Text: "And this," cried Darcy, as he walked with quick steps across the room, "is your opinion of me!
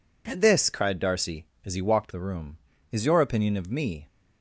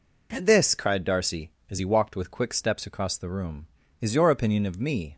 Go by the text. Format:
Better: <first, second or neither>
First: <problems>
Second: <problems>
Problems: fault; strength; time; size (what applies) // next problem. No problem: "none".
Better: second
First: skips "with quick steps across"; at 2.1 s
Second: none